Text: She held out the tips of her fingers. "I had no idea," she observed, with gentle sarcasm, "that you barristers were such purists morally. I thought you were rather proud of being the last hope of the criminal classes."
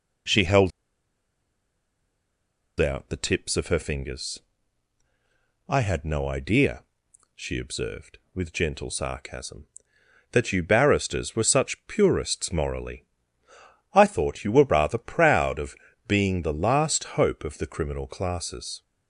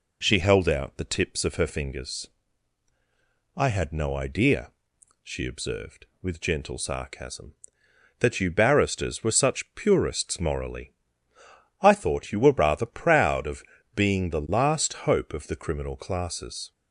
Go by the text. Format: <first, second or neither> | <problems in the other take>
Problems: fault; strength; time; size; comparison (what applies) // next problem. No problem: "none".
second | pauses between "held" and "out"; strong; at 0.7 s; 2.0 s long // pauses between "of" and "being"; slight; at 15.7 s; 0.32 s long; slight in the second